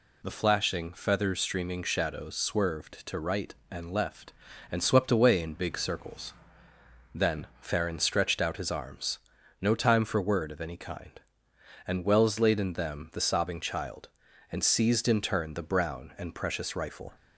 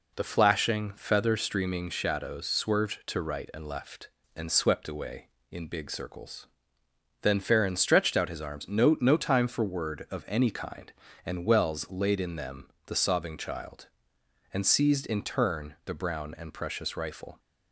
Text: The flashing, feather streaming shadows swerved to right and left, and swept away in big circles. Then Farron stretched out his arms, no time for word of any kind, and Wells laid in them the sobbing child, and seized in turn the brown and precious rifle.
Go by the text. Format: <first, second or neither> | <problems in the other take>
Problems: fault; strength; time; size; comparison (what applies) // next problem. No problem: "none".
first | says "no" twice; at 9.0 s // pauses between "them" and "the"; slight; at 12.6 s; 0.20 s long